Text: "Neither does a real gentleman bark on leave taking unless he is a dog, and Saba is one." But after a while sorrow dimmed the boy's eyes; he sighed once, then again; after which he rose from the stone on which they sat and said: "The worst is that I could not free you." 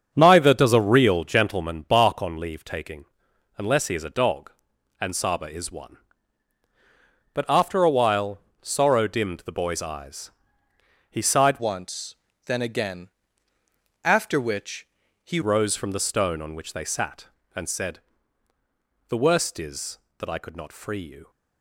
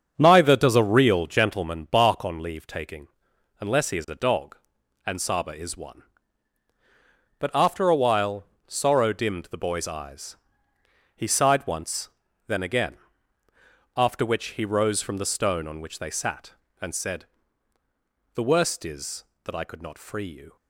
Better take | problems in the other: second | starts louder than the rest; until 1.1 s; 7 dB; also in the second // pauses between "taking" and "unless"; noticeable; at 3.0 s; 0.50 s long; noticeable in the second // pauses between "while" and "sorrow"; slight; at 8.3 s; 0.22 s long; slight in the second // changes voice from "once" to "he"; from 11.5 to 15.3 s; 3.8 s long // pauses between "which" and "he"; at 14.8 s; 0.38 s long

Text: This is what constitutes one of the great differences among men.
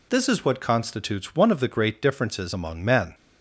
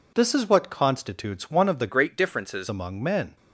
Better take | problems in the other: first | changes voice from "great" to "differences"; from 1.8 to 2.6 s; 0.8 s long

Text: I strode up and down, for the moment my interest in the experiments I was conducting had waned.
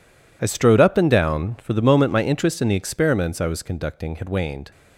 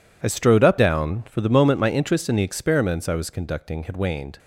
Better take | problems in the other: first | skips "and"; at 0.7 s

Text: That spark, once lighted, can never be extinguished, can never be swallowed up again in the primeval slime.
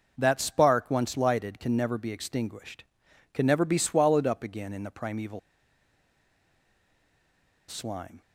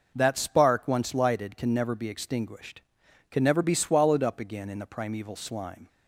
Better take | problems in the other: second | pauses between "primeval" and "slime"; strong; at 5.3 s; 2.2 s long

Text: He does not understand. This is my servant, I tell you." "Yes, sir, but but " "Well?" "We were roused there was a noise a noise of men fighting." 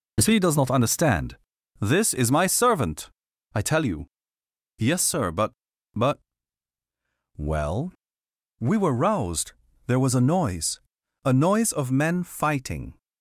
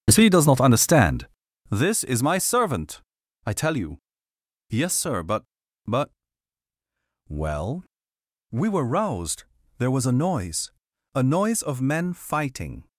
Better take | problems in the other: first | starts louder than the rest; strong; until 1.9 s; 8.5 dB // pauses between "roused" and "there"; slight; at 9.4 s; 0.32 s long; slight in the first // pauses between "noise" and "a"; at 10.7 s; 0.40 s long; also in the first

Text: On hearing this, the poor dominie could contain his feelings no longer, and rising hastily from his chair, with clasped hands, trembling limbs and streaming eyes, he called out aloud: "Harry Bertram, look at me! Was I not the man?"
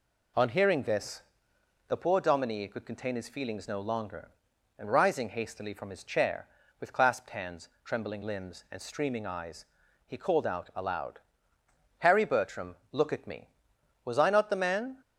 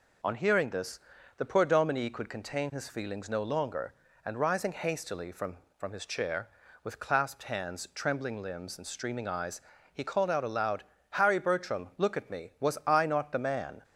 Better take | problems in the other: first | says "from" twice; at 5.7 s

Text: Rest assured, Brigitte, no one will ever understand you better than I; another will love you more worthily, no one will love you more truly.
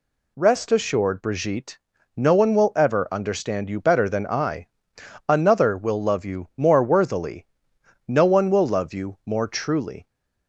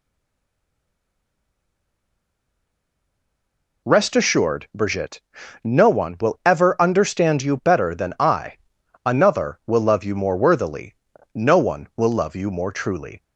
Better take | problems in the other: first | stays silent before the first word; strong; until 3.8 s; 3.8 s long

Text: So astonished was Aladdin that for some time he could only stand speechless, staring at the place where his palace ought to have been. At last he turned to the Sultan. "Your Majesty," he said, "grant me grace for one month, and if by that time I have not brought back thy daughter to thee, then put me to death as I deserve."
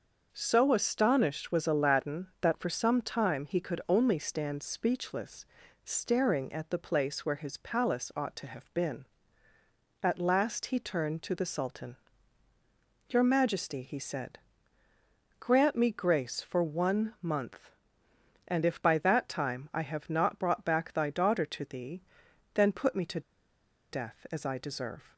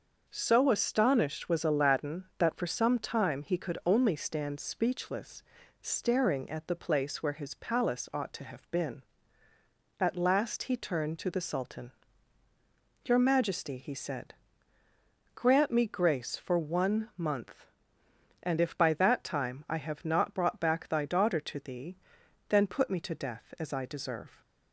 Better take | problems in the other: second | starts louder than the rest; until 1.3 s; 6 dB; also in the second // pauses between "to" and "death"; noticeable; at 23.1 s; 0.70 s long

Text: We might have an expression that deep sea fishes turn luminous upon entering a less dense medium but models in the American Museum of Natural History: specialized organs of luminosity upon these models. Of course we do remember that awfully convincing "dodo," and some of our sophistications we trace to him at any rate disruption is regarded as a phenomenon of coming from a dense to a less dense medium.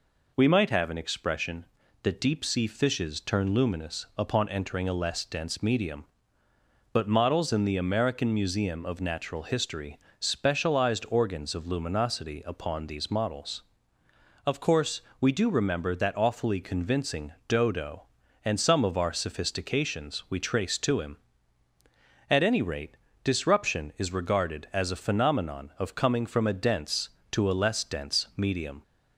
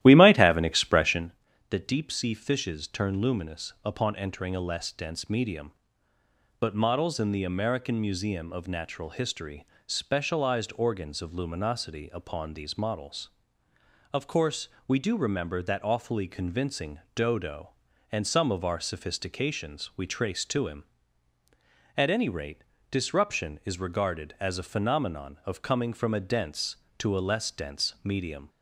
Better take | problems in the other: first | starts louder than the rest; strong; until 1.4 s; 13.5 dB // pauses between "course" and "we"; slight; at 14.6 s; 0.18 s long; slight in the first // pauses between "convincing" and "dodo"; slight; at 16.9 s; 0.16 s long; slight in the first // pauses between "rate" and "disruption"; slight; at 22.6 s; 0.26 s long; slight in the first

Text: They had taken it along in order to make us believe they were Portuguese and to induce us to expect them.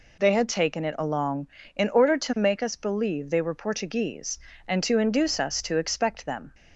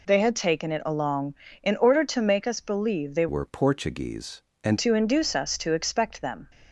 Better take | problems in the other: first | changes voice from "were" to "and"; from 3.2 to 4.7 s; 1.5 s long

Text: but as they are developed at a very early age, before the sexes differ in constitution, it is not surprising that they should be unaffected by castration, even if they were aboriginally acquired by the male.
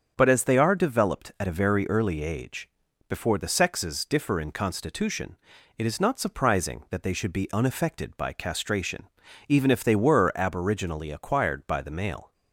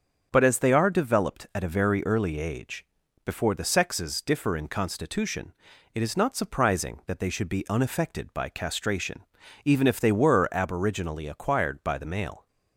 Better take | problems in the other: neither | starts louder than the rest; the same in both

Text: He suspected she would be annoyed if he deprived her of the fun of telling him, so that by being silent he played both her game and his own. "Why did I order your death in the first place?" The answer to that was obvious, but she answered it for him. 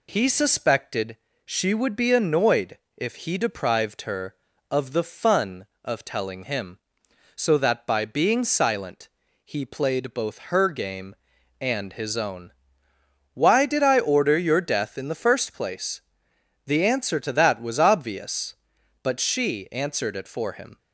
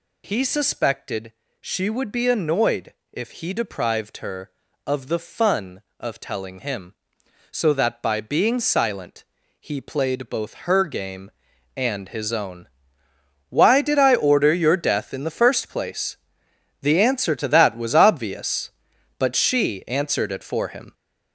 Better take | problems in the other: first | gets louder; throughout; 6.5 dB // pauses between "suspected" and "she"; slight; at 1.3 s; 0.28 s long; slight in the first // pauses between "annoyed" and "if"; slight; at 2.9 s; 0.18 s long; slight in the first // pauses between "silent" and "he"; slight; at 9.2 s; 0.36 s long; slight in the first

